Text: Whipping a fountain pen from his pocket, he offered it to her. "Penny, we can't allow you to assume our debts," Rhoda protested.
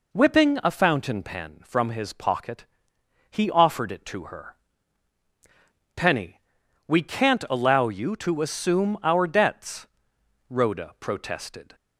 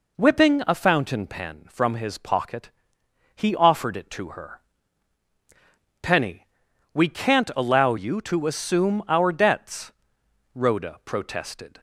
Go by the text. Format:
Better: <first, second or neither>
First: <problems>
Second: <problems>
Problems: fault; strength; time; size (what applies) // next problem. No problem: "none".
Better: neither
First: none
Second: none